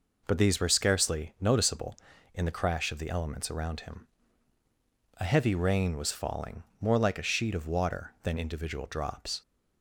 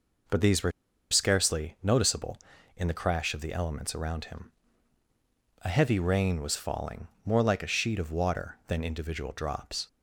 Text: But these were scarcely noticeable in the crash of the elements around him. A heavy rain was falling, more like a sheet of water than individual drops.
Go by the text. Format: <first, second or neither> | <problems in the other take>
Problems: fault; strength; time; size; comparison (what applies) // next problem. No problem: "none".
first | pauses between "were" and "scarcely"; at 0.7 s; 0.40 s long